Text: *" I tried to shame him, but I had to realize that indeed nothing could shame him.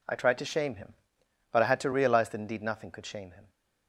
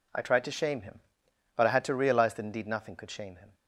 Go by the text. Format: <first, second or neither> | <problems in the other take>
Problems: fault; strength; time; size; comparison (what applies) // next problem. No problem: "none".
neither | none